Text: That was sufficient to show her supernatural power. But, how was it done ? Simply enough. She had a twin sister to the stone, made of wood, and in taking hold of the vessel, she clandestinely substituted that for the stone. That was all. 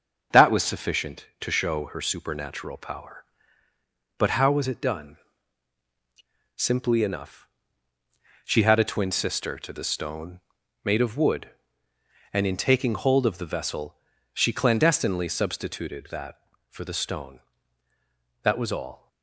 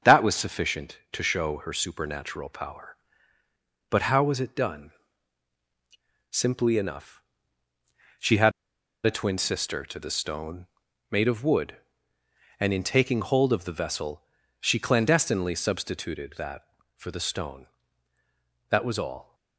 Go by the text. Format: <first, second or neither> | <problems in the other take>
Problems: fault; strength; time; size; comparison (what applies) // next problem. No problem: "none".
first | starts louder than the rest; until 1.2 s; 6.5 dB; also in the first // pauses between "had" and "a"; noticeable; at 8.5 s; 0.54 s long